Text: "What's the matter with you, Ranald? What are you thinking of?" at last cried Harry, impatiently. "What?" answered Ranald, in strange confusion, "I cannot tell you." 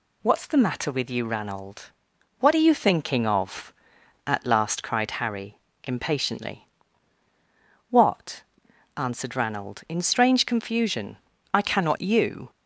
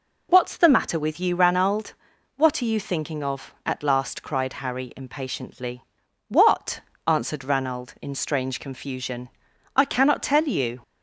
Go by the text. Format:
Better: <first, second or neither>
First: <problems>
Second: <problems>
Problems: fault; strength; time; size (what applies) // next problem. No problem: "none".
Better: second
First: skips "tell"; at 12.0 s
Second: none